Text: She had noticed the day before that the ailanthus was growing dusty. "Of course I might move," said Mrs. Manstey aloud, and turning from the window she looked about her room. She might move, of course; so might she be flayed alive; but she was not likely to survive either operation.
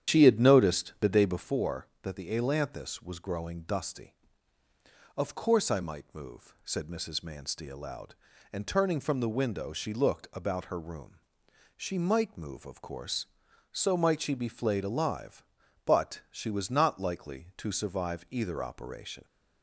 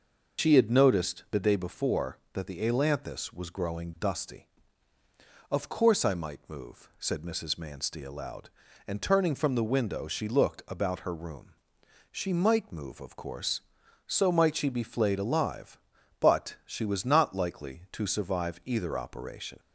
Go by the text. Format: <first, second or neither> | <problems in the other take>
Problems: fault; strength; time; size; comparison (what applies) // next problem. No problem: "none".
second | starts louder than the rest; strong; until 1.6 s; 9.5 dB